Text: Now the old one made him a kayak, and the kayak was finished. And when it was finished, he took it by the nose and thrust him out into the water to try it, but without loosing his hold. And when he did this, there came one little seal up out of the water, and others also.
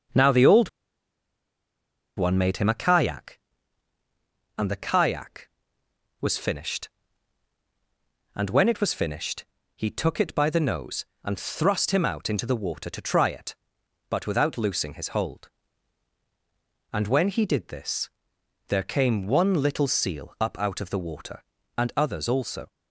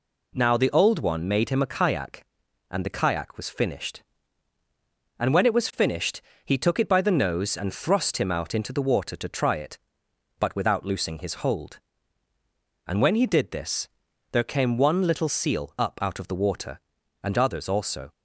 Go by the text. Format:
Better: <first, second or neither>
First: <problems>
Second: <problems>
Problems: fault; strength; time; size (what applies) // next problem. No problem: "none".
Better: second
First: pauses between "old" and "one"; strong; at 0.6 s; 1.4 s long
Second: none